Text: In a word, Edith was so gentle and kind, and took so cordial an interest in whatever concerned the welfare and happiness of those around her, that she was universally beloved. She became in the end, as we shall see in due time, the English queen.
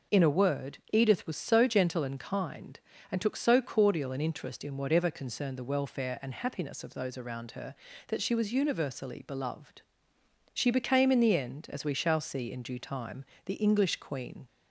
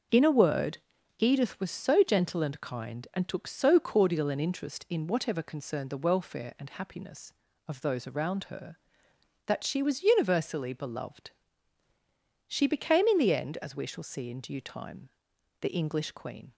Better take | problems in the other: neither | none

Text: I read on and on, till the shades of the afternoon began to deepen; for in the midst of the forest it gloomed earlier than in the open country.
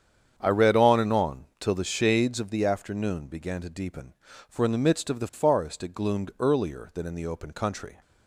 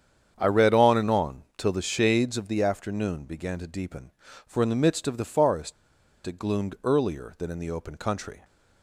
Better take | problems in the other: first | starts louder than the rest; strong; until 1.3 s; 8 dB; strong in the first // pauses between "forest" and "it"; noticeable; at 5.7 s; 0.52 s long

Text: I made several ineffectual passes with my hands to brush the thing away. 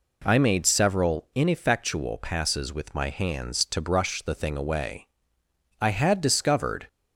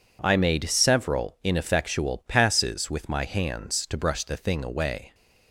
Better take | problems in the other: second | goes on to say "I had discovered"; noticeable; from 5.8 s on; 1.0 s long

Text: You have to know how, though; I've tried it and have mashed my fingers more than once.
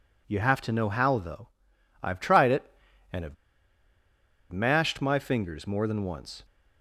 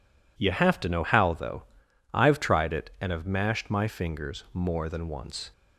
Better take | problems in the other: second | pauses between "have" and "mashed"; at 3.3 s; 1.1 s long

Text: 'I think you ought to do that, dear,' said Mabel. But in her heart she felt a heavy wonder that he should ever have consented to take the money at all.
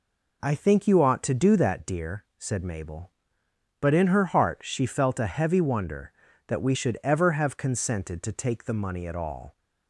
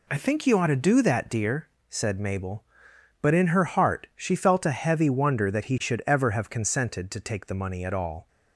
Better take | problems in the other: second | says "we" for "he"; at 6.6 s

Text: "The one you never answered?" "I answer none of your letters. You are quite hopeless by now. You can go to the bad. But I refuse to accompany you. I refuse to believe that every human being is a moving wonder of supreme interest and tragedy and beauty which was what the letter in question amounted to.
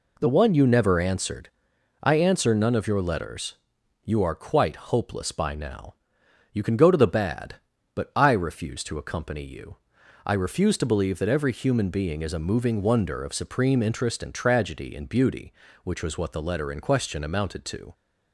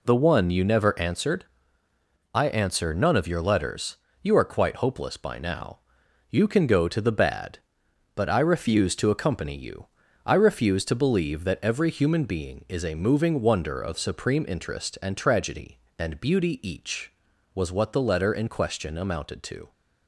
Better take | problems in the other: first | says "each" for "which"; at 16.6 s

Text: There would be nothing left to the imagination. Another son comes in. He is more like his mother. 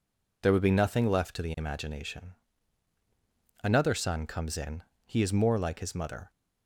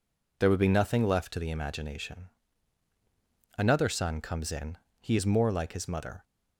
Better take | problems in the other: neither | none

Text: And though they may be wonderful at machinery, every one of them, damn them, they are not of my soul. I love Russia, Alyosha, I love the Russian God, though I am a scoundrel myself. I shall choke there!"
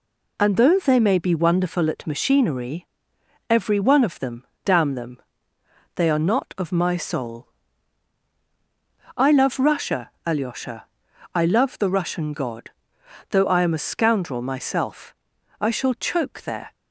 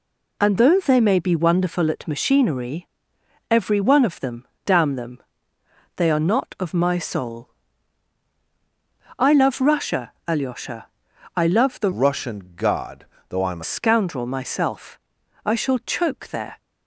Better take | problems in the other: first | changes voice from "Russian" to "a"; from 11.9 to 13.6 s; 1.7 s long

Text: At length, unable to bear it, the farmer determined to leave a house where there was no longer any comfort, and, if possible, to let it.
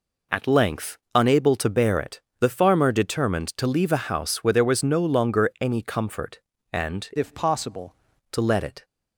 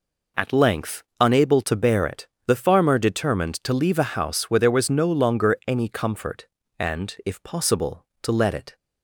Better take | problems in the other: second | changes voice from "if" to "possible"; from 7.1 to 7.9 s; 0.8 s long

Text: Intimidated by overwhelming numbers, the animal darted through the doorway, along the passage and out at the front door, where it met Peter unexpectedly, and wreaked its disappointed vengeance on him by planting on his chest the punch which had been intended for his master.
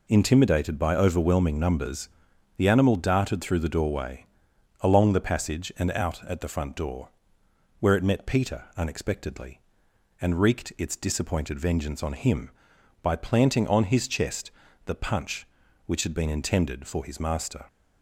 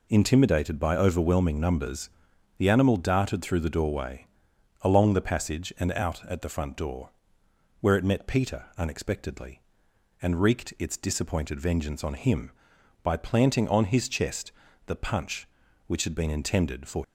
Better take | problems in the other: first | pauses between "chest" and "the"; slight; at 14.5 s; 0.36 s long; slight in the first // stops before "his master"; at 17.0 s

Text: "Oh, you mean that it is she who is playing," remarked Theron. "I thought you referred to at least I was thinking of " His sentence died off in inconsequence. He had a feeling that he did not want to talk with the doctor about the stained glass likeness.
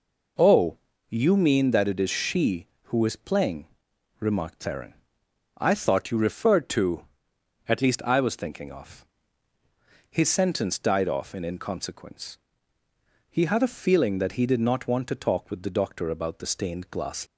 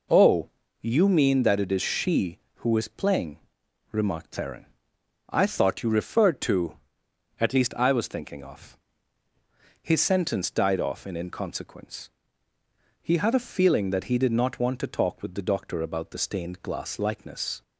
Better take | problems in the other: second | stops before "likeness"; at 17.2 s

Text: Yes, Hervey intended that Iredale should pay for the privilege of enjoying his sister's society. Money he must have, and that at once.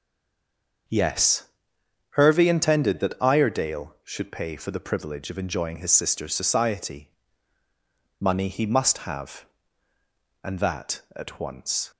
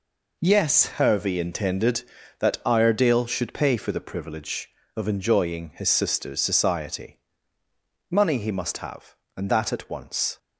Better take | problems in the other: second | stays silent before the first word; slight; until 0.8 s; 0.8 s long // starts louder than the rest; until 2.5 s; 6.5 dB

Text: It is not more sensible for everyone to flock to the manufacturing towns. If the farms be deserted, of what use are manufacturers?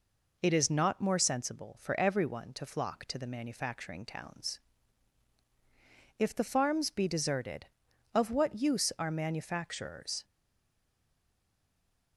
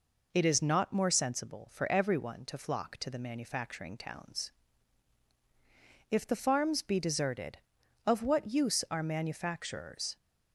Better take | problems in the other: second | stays silent after the last word; noticeable; from 10.2 s on; 1.9 s long

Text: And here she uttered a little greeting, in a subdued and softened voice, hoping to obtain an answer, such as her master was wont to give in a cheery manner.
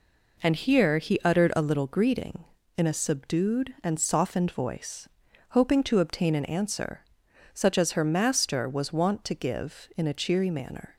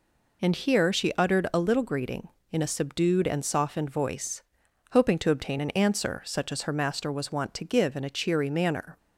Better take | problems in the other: second | says "he" for "she"; at 0.9 s

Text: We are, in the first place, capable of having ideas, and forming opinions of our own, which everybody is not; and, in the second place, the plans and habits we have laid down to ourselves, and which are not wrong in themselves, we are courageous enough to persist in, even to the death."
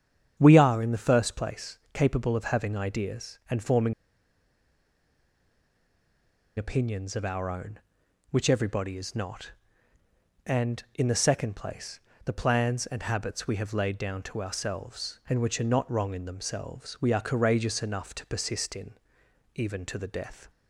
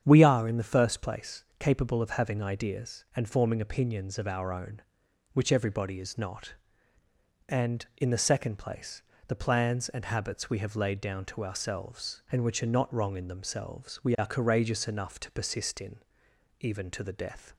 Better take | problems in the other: second | starts louder than the rest; strong; until 1.3 s; 8 dB; strong in the second // pauses between "forming" and "opinions"; strong; at 3.9 s; 2.6 s long

